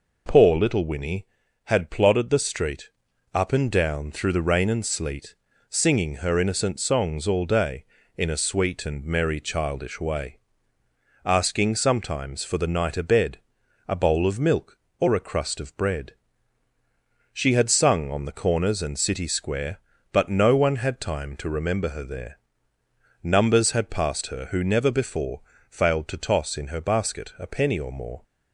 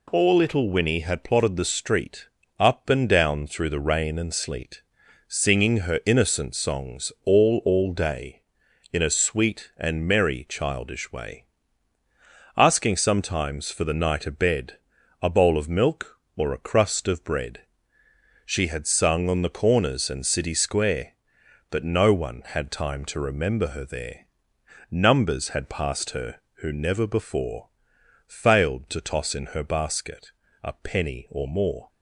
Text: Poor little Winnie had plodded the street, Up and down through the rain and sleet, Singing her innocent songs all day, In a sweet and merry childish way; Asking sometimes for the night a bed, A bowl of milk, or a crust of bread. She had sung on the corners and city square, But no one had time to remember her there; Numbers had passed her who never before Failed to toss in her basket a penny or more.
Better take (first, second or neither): first